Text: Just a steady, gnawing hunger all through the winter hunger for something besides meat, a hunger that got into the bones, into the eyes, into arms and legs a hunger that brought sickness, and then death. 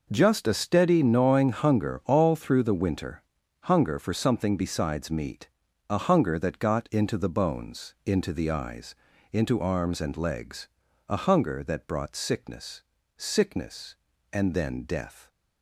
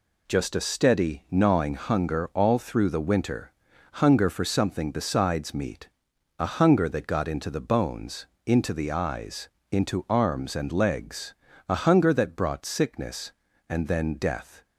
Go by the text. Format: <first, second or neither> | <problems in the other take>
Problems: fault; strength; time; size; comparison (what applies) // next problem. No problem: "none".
second | pauses between "winter" and "hunger"; at 3.2 s; 0.44 s long; noticeable in the second // pauses between "legs" and "a"; at 10.6 s; 0.42 s long; slight in the second // says "sickness" twice; at 13.1 s